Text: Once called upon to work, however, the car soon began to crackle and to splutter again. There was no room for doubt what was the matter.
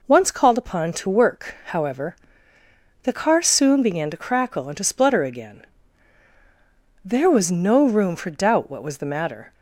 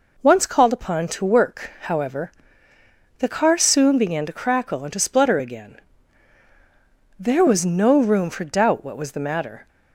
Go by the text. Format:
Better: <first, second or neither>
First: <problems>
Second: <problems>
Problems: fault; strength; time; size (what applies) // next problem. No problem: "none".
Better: neither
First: none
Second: none